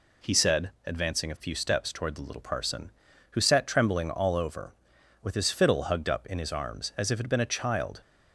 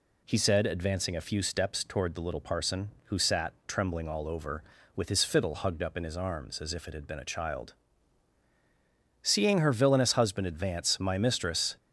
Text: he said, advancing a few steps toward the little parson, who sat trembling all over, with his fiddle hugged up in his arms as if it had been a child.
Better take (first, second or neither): first